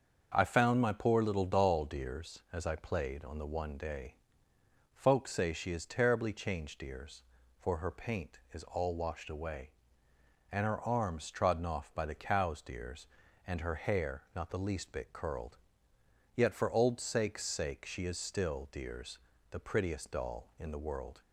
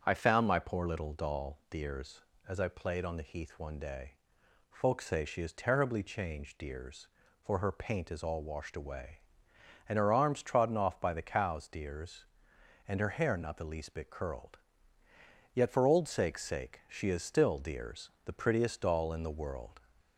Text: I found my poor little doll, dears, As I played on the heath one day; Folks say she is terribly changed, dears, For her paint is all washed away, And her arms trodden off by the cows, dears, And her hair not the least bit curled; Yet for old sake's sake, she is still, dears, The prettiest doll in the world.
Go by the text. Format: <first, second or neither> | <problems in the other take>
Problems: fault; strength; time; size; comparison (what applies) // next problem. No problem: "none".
second | starts louder than the rest; until 1.3 s; 6.5 dB; also in the second // skips "heath"; at 3.4 s